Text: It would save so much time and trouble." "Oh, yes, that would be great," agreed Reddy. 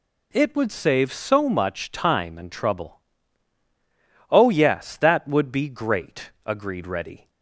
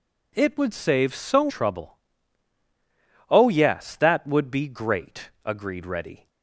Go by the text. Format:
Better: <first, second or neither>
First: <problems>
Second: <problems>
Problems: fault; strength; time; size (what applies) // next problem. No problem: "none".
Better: first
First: none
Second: skips "much time and"; at 1.4 s